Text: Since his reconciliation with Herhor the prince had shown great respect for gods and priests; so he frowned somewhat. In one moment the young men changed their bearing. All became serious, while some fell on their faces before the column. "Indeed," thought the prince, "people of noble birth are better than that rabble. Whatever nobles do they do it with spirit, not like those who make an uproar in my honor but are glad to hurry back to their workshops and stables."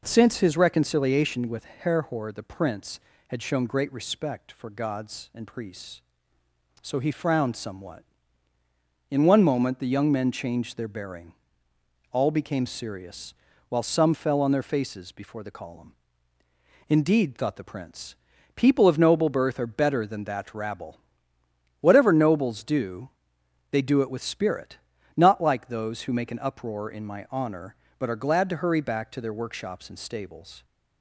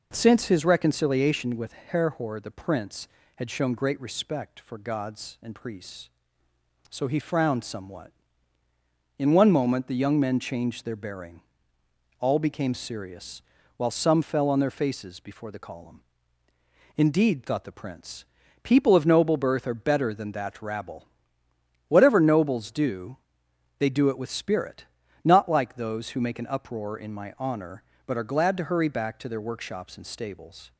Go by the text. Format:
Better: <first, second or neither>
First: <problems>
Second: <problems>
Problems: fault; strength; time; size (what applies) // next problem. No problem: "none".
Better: neither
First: pauses between "do" and "they"; noticeable; at 23.0 s; 0.62 s long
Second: pauses between "do" and "they"; noticeable; at 23.1 s; 0.62 s long